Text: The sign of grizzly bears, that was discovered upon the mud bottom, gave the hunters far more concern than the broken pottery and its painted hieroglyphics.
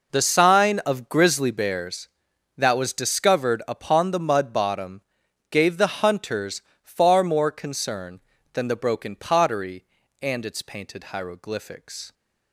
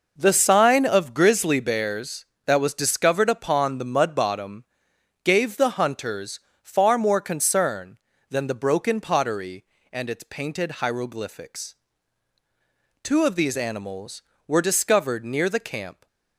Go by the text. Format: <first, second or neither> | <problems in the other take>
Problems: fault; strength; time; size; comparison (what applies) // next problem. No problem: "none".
first | pauses between "hunters" and "far"; slight; at 6.3 s; 0.24 s long; slight in the first // goes on to say "Two of these animals were discovered near the camp"; strong; from 13.0 s on; 3.0 s long